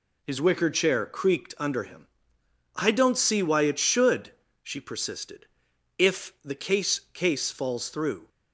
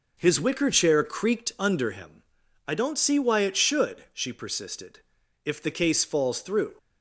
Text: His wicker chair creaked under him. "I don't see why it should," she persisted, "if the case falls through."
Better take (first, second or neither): second